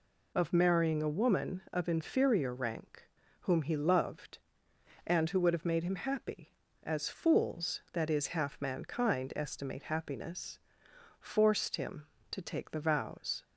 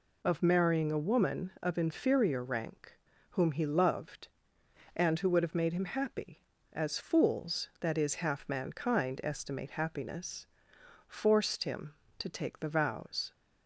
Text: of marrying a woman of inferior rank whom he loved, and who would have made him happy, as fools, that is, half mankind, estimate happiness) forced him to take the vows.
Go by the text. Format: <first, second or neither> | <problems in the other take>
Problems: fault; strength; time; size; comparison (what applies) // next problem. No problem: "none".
neither | pauses between "rank" and "whom"; slight; the same in both